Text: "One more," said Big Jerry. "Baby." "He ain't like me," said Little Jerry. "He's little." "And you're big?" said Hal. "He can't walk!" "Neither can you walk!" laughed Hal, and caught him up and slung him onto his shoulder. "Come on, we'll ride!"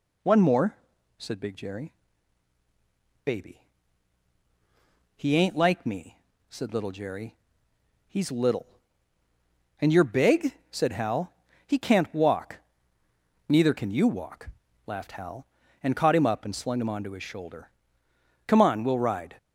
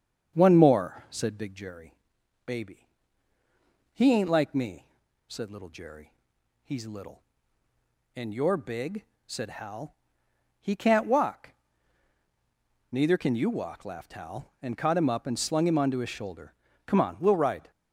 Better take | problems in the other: first | starts louder than the rest; strong; until 1.8 s; 7.5 dB

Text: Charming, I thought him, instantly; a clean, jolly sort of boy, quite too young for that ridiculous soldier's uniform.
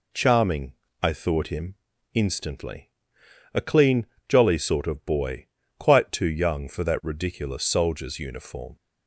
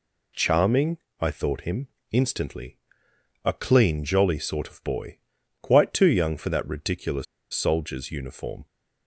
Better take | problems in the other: first | pauses between "ridiculous" and "soldier's"; slight; at 7.2 s; 0.28 s long

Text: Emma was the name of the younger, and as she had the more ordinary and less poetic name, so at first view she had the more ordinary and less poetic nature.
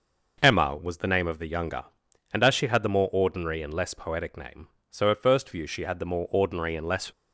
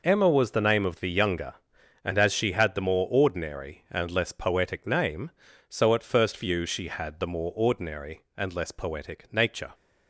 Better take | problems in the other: second | stops before "poetic nature"; at 7.1 s

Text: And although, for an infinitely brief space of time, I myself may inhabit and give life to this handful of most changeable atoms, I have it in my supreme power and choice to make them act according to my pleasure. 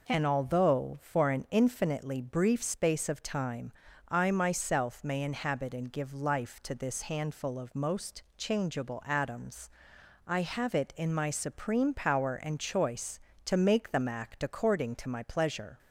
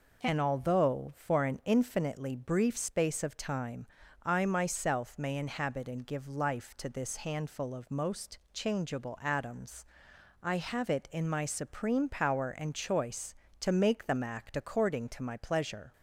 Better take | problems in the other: neither | pauses between "most" and "changeable"; slight; the same in both

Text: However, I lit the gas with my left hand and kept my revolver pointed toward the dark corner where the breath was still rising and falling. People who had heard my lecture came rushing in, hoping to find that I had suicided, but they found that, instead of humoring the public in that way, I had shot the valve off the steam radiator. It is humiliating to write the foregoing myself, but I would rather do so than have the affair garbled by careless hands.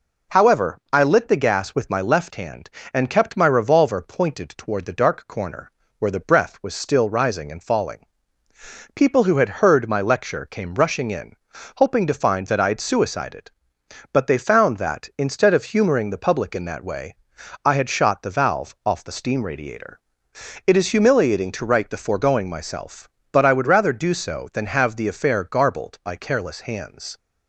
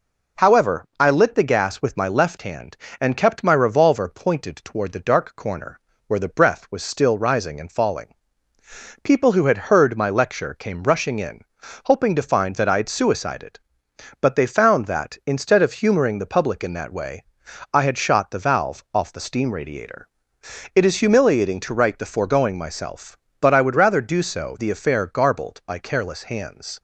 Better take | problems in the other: first | pauses between "corner" and "where"; slight; at 5.7 s; 0.28 s long; slight in the first // skips "than have"; at 24.5 s

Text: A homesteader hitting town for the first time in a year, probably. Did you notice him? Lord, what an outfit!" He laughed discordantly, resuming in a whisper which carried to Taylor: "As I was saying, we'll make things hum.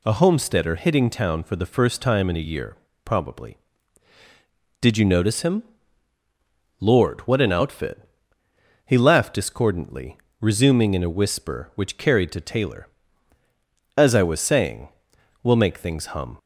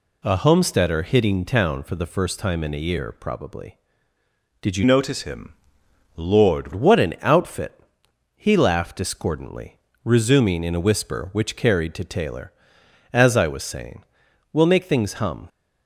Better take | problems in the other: first | changes voice from "notice" to "Lord"; from 4.8 to 6.7 s; 1.9 s long

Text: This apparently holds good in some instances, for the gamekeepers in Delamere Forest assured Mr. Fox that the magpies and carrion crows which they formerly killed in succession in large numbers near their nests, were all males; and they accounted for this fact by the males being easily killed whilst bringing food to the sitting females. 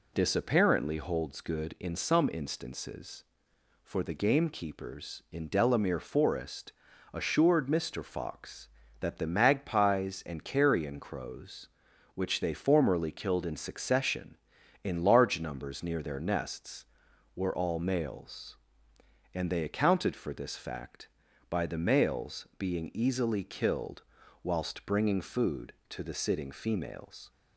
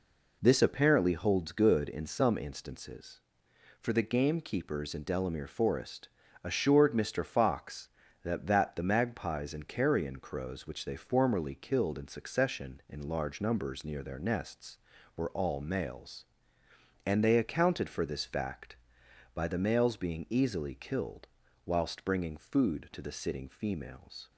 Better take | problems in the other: first | pauses between "Forest" and "assured"; slight; at 6.0 s; 0.34 s long; also in the first // says "that" twice; at 8.4 s // pauses between "killed" and "whilst"; at 21.2 s; 0.40 s long; also in the first

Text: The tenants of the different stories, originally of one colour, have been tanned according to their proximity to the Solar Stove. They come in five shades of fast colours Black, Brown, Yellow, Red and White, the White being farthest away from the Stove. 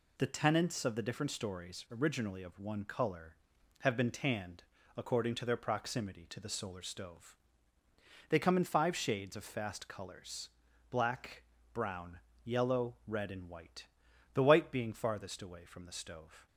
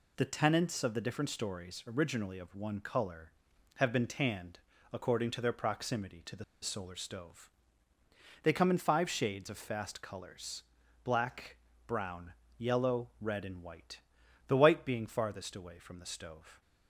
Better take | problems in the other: first | pauses between "tanned" and "according"; slight; at 4.5 s; 0.34 s long; slight in the first // pauses between "the" and "Solar"; slight; at 6.4 s; 0.18 s long // pauses between "colours" and "Black"; at 10.6 s; 0.40 s long; also in the first

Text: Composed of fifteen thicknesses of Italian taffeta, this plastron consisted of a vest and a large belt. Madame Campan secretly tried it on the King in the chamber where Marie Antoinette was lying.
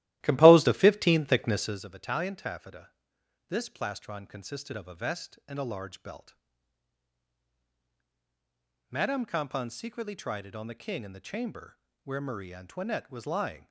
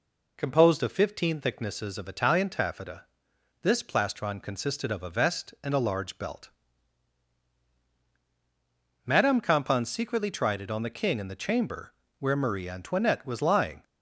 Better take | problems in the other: second | starts louder than the rest; strong; until 1.8 s; 15 dB // pauses between "chamber" and "where"; slight; at 11.7 s; 0.24 s long; slight in the second

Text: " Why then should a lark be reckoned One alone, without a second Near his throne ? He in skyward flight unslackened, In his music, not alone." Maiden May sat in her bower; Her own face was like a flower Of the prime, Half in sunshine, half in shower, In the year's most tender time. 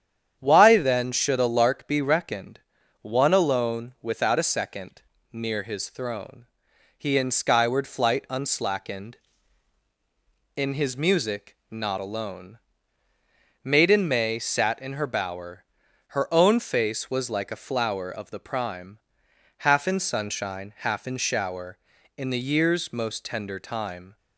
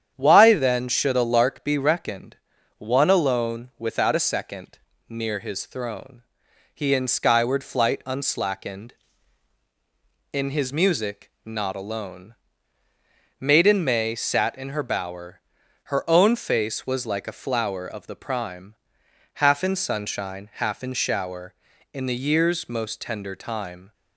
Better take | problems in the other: neither | starts louder than the rest; strong; the same in both // pauses between "reckoned" and "One"; the same in both // pauses between "second" and "Near"; slight; the same in both

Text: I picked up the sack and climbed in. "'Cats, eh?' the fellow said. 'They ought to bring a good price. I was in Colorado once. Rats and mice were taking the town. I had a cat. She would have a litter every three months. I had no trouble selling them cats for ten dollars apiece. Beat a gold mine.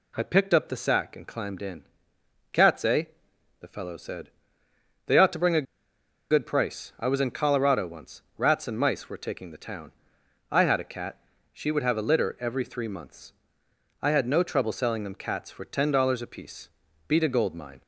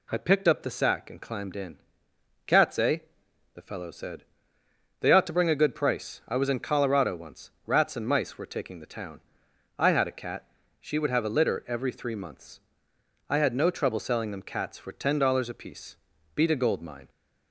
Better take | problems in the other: second | pauses between "a" and "good"; noticeable; at 5.6 s; 0.66 s long

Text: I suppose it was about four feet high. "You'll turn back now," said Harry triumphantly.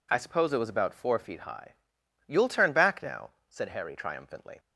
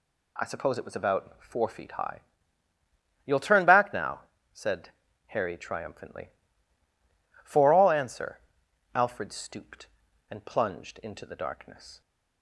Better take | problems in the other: first | pauses between "said" and "Harry"; at 4.9 s; 0.38 s long // goes on to say "For all answer Alfred stooped and plunged into the darkness"; strong; from 7.4 s on; 4.5 s long

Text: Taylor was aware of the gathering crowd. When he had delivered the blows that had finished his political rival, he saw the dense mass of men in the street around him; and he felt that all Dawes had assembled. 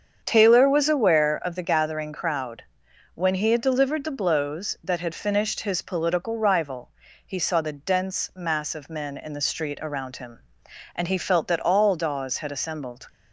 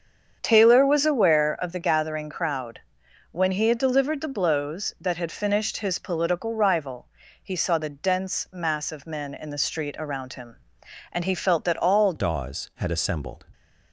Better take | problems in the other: first | starts louder than the rest; strong; until 1.4 s; 7.5 dB; strong in the first // changes voice at "Dawes"; from 12.1 s on; 1.3 s long

